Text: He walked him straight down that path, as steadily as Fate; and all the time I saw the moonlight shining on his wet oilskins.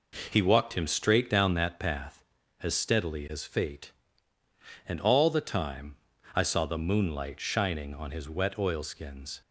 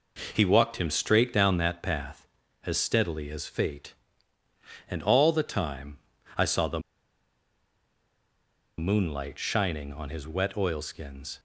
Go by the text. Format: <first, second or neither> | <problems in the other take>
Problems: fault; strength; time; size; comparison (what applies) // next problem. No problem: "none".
first | pauses between "time" and "I"; slight; at 5.9 s; 0.36 s long; slight in the first // pauses between "the" and "moonlight"; strong; at 6.7 s; 1.9 s long